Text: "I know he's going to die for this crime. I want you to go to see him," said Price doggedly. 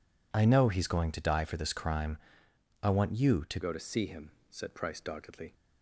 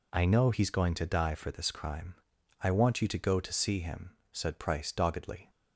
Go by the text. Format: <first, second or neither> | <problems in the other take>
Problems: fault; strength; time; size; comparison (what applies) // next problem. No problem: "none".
second | changes voice at "go"; from 3.6 s on; 1.9 s long